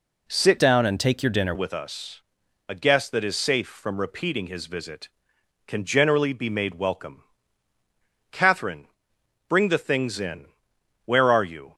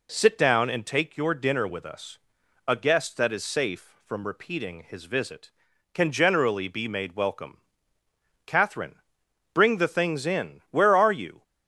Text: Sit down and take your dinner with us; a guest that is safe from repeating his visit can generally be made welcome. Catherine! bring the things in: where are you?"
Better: second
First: changes voice from "down" to "dinner"; from 0.5 to 1.5 s; 1.0 s long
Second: none

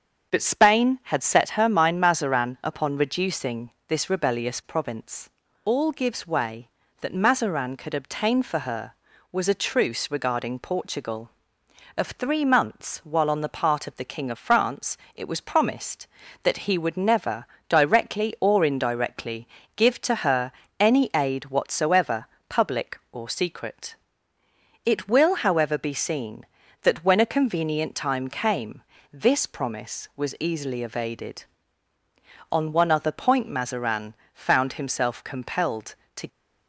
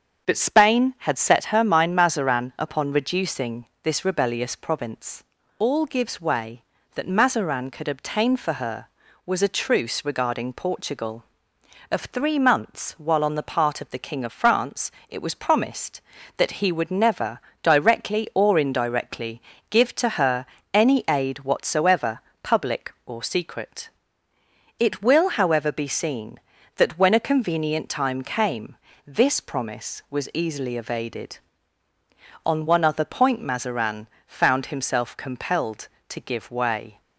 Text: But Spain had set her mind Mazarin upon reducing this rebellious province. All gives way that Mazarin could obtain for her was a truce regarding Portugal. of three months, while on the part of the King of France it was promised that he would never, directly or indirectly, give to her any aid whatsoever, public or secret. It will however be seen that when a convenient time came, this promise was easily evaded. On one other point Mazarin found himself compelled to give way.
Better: second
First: starts louder than the rest; strong; until 1.3 s; 7 dB // pauses between "reducing" and "this"; slight; at 3.6 s; 0.18 s long // pauses between "France" and "it"; slight; at 14.9 s; 0.18 s long // pauses between "her" and "any"; slight; at 20.5 s; 0.28 s long // pauses between "Mazarin" and "found"; slight; at 34.1 s; 0.22 s long // stops before "give way"; at 36.2 s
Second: starts louder than the rest; strong; until 1.3 s; 7 dB // pauses between "reducing" and "this"; slight; at 3.6 s; 0.18 s long // pauses between "France" and "it"; slight; at 14.9 s; 0.18 s long // pauses between "her" and "any"; slight; at 20.4 s; 0.28 s long // pauses between "Mazarin" and "found"; slight; at 34.0 s; 0.22 s long

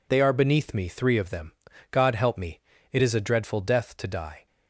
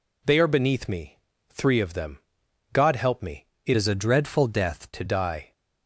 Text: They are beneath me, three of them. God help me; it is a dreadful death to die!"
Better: first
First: none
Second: changes voice from "is" to "to"; from 3.7 to 5.0 s; 1.3 s long

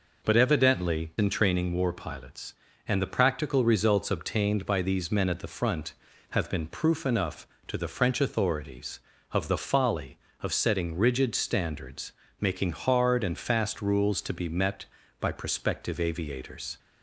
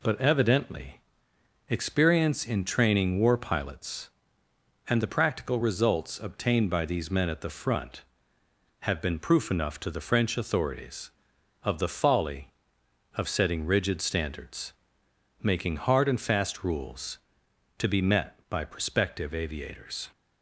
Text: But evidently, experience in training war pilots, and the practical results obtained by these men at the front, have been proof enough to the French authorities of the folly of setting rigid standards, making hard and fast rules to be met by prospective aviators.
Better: second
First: skips "experience"; at 1.1 s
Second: none

